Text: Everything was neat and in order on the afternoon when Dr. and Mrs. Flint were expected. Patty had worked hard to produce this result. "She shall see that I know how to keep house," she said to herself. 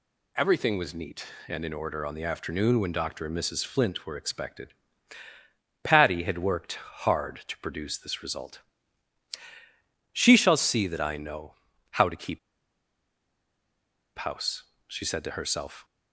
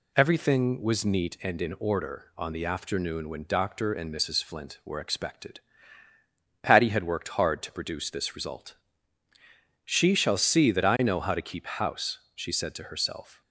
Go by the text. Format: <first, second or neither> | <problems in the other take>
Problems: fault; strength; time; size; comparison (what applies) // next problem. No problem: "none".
second | pauses between "know" and "how"; slight; at 11.5 s; 0.36 s long // pauses between "keep" and "house"; strong; at 12.3 s; 1.7 s long